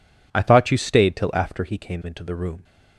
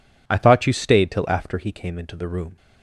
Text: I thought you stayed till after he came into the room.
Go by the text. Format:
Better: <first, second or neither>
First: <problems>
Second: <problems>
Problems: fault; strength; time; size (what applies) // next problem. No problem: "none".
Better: neither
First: none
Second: none